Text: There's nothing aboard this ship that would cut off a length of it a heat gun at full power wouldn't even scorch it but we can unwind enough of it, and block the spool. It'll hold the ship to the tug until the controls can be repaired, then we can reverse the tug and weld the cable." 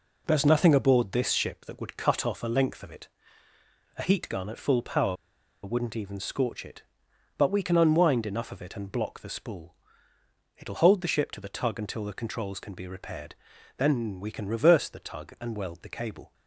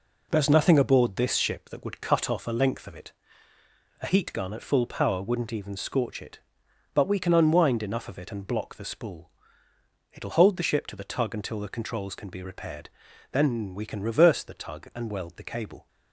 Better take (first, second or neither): second